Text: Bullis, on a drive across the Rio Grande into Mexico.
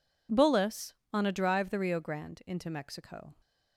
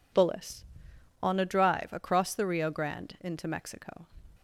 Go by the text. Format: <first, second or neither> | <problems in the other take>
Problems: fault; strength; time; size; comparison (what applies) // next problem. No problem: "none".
second | skips "across"; at 1.6 s